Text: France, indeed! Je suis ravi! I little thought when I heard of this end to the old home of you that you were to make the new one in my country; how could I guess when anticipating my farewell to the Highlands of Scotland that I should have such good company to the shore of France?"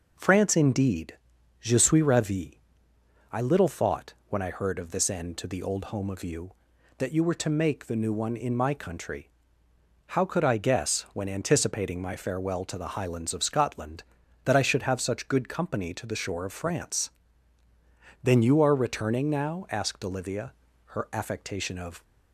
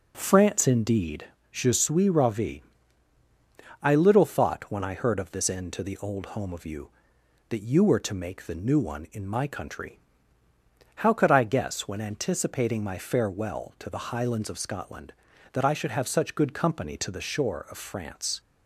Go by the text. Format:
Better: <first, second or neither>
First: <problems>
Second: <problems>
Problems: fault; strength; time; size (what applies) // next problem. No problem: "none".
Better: second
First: goes on to say "Then you are returning now asked Olivia her affectation of"; strong; from 18.2 s on; 3.8 s long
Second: none